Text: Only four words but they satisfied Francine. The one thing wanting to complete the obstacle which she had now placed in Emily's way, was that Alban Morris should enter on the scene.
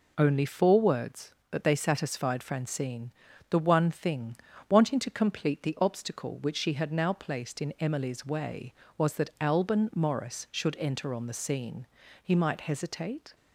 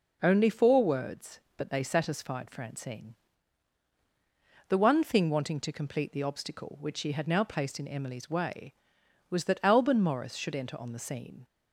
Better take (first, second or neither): second